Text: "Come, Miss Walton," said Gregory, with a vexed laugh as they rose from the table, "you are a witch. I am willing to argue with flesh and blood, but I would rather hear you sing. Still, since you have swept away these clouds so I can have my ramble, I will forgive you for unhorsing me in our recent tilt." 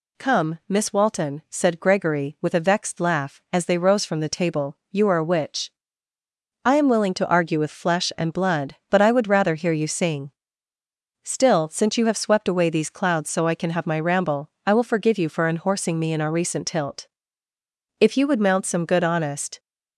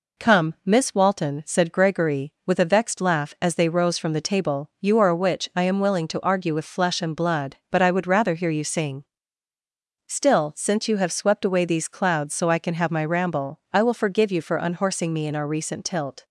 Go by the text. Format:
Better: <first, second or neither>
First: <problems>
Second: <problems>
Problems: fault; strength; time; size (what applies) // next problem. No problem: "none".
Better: second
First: goes on to say "If you would mount some good honest"; from 17.9 s on; 1.6 s long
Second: none